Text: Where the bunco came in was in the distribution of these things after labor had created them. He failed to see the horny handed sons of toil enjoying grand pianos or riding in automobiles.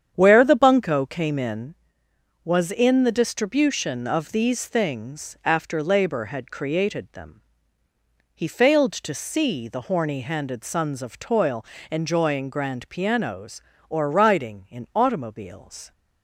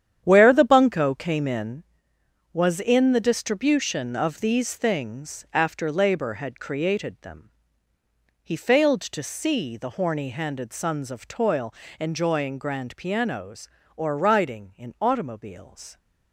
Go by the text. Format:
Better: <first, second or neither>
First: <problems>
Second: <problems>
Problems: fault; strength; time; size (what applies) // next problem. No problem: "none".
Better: first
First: starts louder than the rest; strong; until 1.1 s; 8.5 dB // pauses between "toil" and "enjoying"; slight; at 11.6 s; 0.26 s long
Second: gets quieter; strong; throughout; 10.5 dB // starts louder than the rest; strong; until 1.2 s; 9.5 dB // pauses between "toil" and "enjoying"; slight; at 11.7 s; 0.26 s long